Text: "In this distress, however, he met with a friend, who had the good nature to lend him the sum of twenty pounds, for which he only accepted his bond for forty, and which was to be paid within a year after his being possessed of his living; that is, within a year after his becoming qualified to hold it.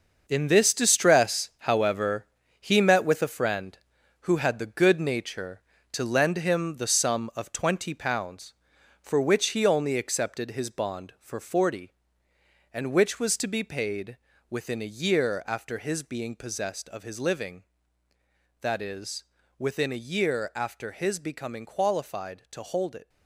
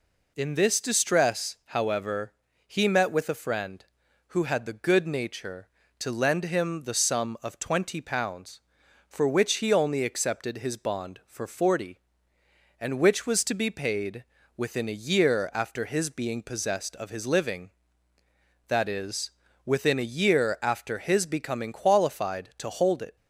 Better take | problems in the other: second | gets quieter; strong; throughout; 9 dB // pauses between "paid" and "within"; slight; at 14.1 s; 0.32 s long; slight in the second

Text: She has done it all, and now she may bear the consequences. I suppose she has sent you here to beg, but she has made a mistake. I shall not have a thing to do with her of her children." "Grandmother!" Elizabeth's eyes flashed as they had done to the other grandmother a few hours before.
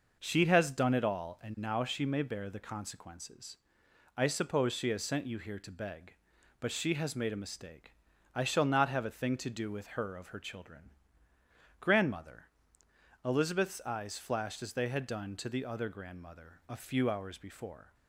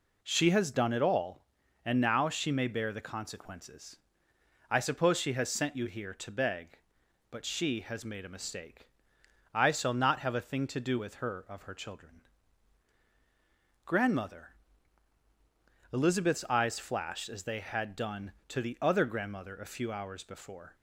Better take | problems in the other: neither | none

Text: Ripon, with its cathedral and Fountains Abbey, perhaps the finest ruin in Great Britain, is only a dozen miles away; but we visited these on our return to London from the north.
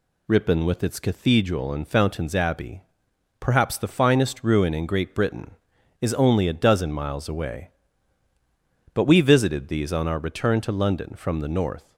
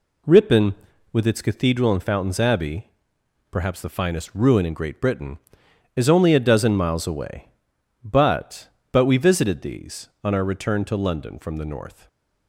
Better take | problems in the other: first | says "but" twice; at 8.9 s // stays silent after the last word; slight; from 11.9 s on; 0.5 s long

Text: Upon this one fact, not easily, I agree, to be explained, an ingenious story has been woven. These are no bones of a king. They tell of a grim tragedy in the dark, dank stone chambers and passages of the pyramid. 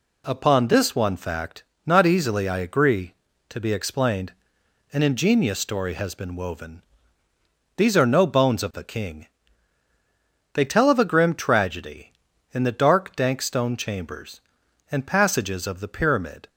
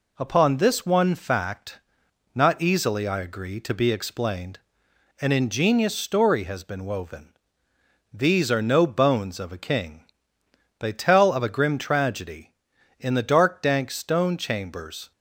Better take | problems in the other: first | stops before "and passages of the pyramid"; at 15.1 s

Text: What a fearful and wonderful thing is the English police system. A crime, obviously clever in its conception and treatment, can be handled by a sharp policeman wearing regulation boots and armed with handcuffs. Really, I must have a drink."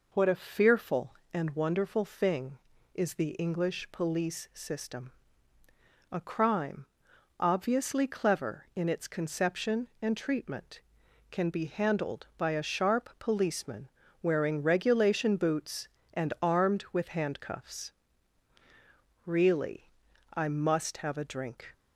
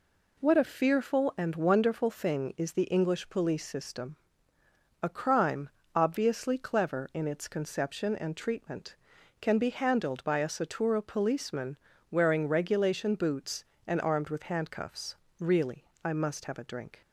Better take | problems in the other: first | says "satura" for "sharp"; at 10.4 s // pauses between "policeman" and "wearing"; slight; at 11.7 s; 0.36 s long; slight in the first

